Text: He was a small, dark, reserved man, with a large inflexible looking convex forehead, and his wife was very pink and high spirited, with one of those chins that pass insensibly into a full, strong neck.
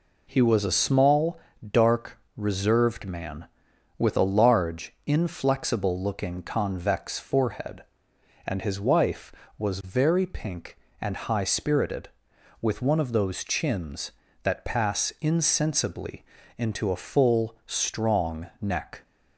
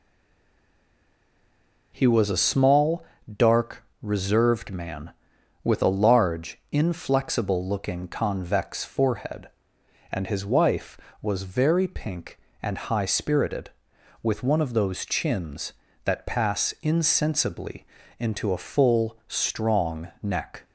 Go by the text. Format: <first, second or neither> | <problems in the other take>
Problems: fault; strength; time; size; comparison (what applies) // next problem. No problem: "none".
first | stays silent before the first word; noticeable; until 1.9 s; 1.9 s long // pauses between "insensibly" and "into"; slight; at 17.8 s; 0.34 s long; slight in the first